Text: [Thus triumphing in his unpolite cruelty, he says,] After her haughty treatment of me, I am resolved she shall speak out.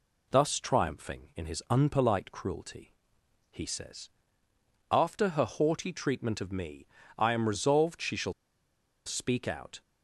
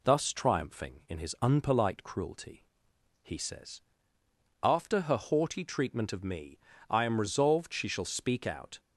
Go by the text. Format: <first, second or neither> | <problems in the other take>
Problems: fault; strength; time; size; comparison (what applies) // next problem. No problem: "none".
second | pauses between "shall" and "speak"; noticeable; at 8.3 s; 0.73 s long